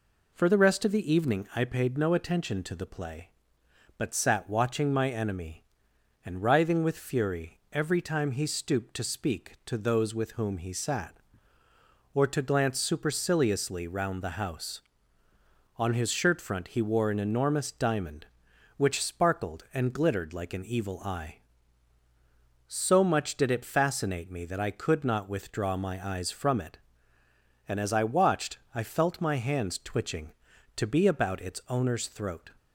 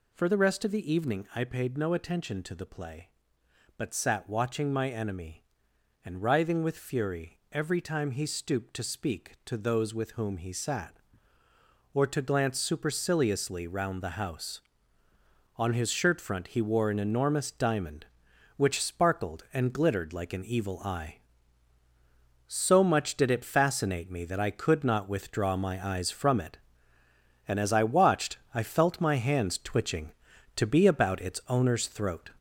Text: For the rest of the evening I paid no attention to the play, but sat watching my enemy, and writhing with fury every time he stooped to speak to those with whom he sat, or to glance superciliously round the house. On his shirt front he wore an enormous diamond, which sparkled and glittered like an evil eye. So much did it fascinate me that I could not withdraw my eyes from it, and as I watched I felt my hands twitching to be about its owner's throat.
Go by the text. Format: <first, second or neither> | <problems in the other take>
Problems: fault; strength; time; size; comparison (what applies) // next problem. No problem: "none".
first | gets louder; noticeable; throughout; 5.5 dB // pauses between "watched" and "I"; slight; at 28.3 s; 0.18 s long; slight in the first